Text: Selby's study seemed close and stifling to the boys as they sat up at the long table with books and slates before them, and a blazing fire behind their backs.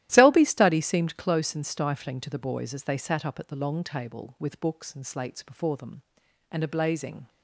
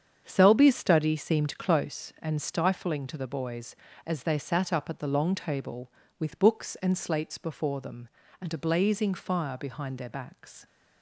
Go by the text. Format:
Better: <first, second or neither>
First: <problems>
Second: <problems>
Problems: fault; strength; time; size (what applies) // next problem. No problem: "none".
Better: second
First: starts louder than the rest; strong; until 1.1 s; 13.5 dB // stops before "fire behind their backs"; at 7.2 s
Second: starts louder than the rest; strong; until 1.2 s; 7.5 dB